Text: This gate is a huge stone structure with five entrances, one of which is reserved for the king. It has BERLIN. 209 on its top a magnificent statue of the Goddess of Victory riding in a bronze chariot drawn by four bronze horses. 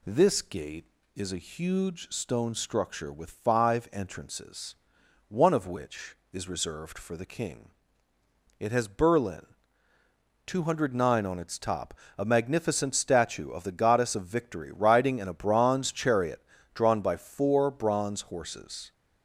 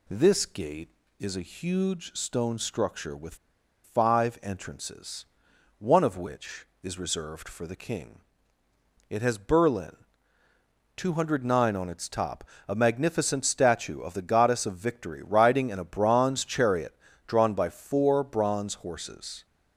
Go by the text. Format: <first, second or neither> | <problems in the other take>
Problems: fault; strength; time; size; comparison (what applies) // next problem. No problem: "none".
first | pauses between "with" and "five"; noticeable; at 3.3 s; 0.49 s long // pauses between "top" and "a"; slight; at 12.4 s; 0.24 s long; slight in the first // pauses between "chariot" and "drawn"; slight; at 16.9 s; 0.32 s long; slight in the first